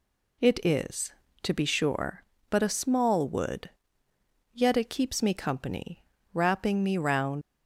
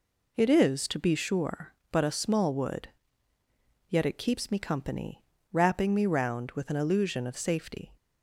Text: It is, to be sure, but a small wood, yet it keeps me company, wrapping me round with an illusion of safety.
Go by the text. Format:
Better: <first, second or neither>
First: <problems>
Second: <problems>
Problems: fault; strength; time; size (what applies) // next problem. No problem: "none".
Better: second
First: stops before "with an illusion of safety"; at 7.4 s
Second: none